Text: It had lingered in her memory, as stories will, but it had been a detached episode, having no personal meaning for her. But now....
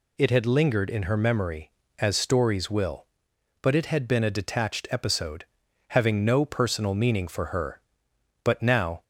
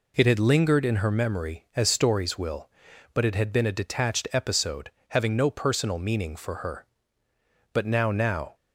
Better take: first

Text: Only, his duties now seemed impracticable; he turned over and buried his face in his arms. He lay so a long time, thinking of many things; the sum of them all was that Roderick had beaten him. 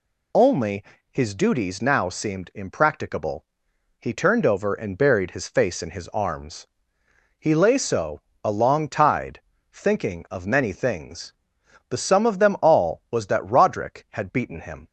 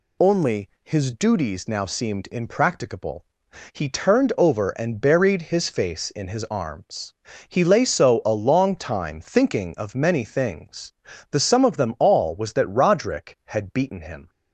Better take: second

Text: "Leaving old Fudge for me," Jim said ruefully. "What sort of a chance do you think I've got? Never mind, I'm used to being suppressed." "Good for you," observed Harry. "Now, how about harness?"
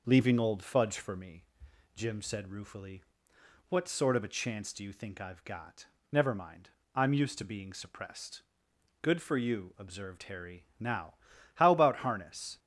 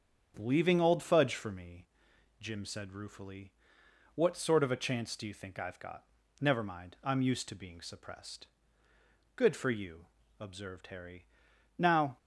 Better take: first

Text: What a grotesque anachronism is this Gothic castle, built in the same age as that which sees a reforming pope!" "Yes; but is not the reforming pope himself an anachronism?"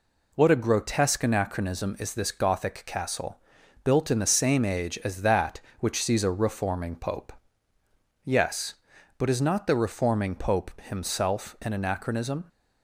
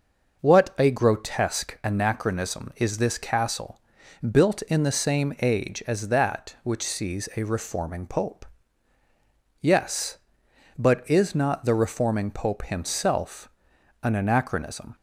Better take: first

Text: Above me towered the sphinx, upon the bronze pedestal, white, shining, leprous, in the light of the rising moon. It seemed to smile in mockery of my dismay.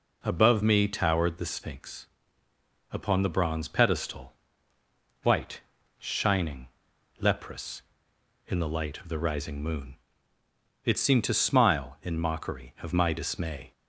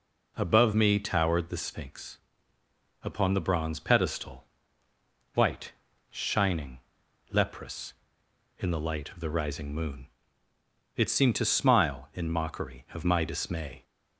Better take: neither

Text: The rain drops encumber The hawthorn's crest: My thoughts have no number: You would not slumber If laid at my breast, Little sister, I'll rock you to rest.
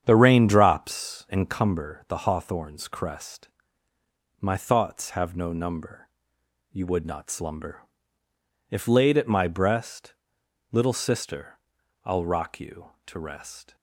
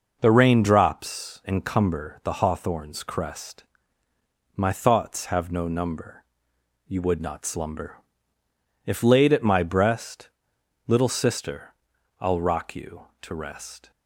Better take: second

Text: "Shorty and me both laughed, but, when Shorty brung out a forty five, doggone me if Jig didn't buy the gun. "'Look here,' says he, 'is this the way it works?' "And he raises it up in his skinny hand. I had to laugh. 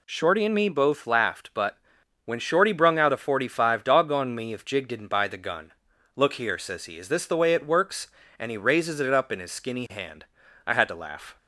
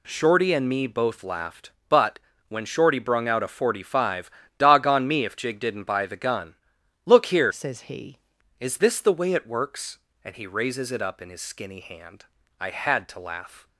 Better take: first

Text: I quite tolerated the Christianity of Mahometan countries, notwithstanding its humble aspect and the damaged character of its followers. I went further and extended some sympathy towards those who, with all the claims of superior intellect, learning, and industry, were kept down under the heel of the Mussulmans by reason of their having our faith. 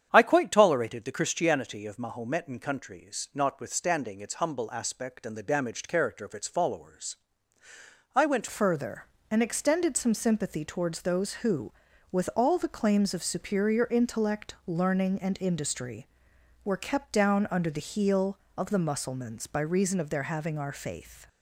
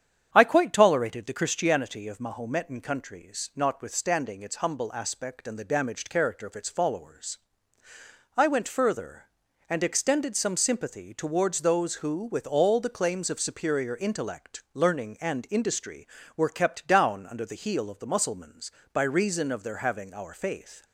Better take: second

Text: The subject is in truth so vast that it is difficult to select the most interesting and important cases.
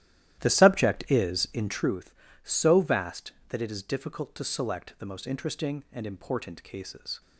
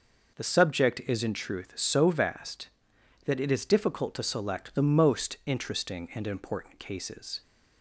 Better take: second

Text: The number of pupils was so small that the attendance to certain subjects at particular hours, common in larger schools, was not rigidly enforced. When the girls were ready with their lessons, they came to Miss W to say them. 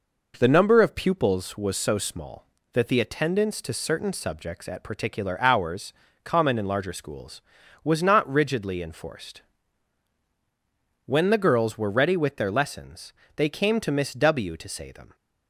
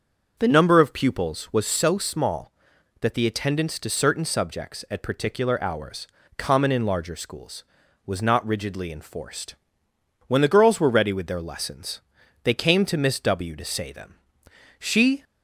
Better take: first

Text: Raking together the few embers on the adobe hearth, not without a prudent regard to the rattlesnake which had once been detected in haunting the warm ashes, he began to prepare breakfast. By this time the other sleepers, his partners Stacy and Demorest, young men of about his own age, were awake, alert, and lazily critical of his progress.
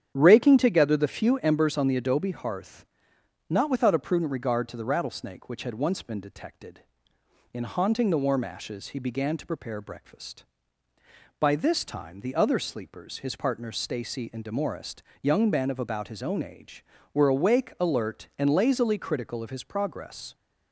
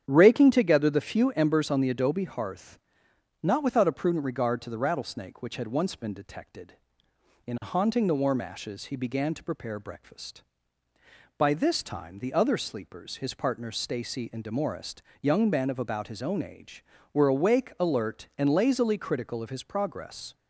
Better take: neither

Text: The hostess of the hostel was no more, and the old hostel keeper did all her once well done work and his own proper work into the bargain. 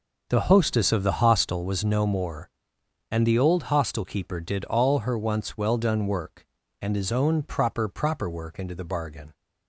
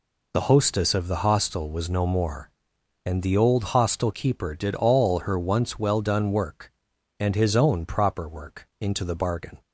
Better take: second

